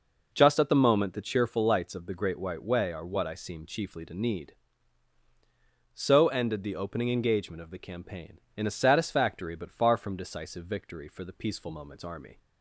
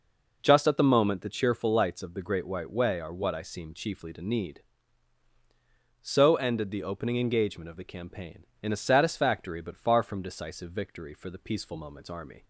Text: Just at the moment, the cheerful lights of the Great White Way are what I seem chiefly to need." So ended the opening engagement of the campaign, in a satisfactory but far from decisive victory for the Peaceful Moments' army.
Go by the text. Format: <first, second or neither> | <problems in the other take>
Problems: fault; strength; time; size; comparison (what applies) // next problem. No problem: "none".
neither | none